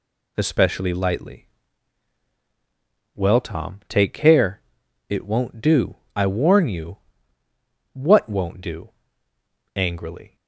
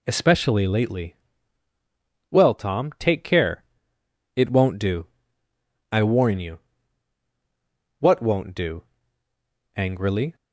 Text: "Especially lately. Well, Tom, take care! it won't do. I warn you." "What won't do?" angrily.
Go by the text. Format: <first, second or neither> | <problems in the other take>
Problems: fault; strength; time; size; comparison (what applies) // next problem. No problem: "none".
second | says "lightly" for "lately"; at 0.9 s